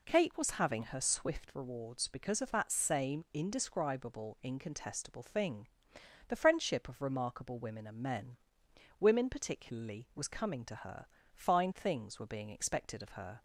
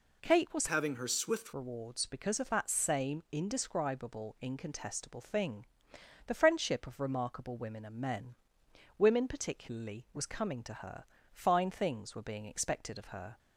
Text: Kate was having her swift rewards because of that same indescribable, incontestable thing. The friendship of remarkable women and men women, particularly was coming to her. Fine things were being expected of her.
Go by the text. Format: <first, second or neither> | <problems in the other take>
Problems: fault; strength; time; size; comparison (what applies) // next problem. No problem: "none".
first | changes voice from "having" to "swift"; from 0.6 to 1.5 s; 0.9 s long // pauses between "men" and "women"; noticeable; at 8.3 s; 0.64 s long; noticeable in the first